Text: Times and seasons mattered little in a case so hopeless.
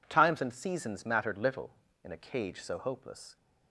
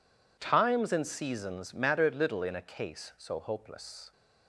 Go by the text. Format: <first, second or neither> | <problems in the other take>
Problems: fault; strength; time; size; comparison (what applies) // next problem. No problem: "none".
second | says "cage" for "case"; at 2.1 s